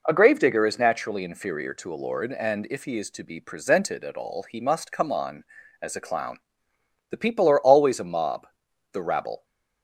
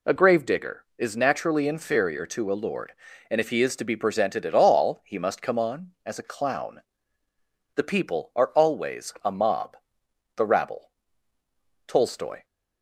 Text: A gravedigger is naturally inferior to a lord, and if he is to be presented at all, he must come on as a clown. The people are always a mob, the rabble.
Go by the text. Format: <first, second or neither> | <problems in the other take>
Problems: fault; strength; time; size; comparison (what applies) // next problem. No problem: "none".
first | goes on to say "Tolstoy"; from 11.8 s on; 0.58 s long